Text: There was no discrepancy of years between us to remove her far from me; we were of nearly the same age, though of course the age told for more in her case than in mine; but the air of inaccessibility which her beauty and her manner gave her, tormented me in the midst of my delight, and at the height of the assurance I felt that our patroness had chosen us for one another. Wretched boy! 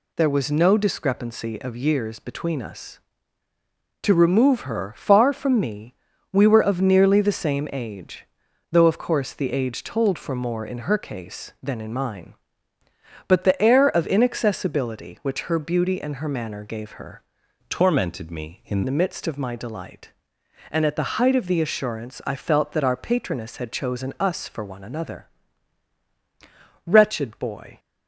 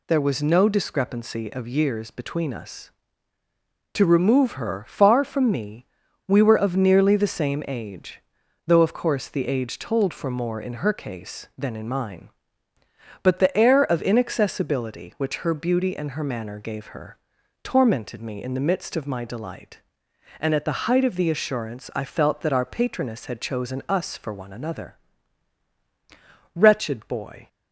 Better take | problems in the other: second | changes voice from "tormented" to "in"; from 17.6 to 18.8 s; 1.2 s long

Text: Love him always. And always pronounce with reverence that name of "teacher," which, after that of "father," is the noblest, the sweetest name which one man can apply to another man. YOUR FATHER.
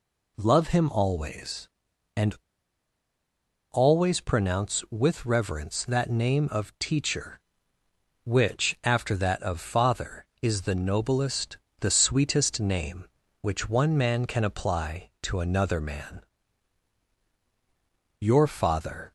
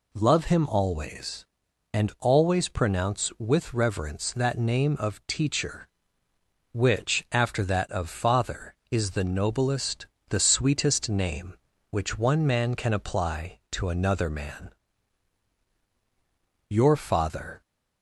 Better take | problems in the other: second | pauses between "And" and "always"; strong; at 2.3 s; 1.3 s long

